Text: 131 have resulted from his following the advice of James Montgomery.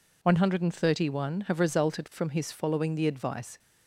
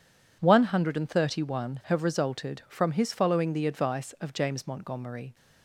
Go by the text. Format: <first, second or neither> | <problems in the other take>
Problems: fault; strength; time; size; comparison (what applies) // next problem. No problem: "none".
second | stops before "of James Montgomery"; at 3.5 s